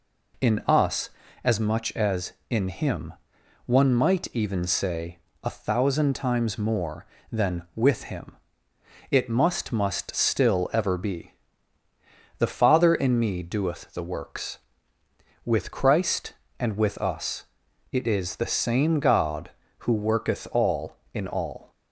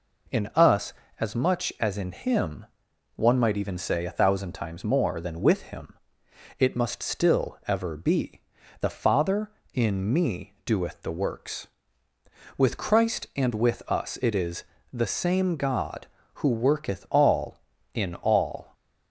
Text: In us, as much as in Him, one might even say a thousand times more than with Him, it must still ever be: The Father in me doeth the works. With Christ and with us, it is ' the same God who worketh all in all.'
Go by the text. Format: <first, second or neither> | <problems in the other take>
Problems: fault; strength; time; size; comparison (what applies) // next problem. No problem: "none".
second | pauses between "say" and "a"; slight; at 5.1 s; 0.26 s long // says "must" twice; at 9.7 s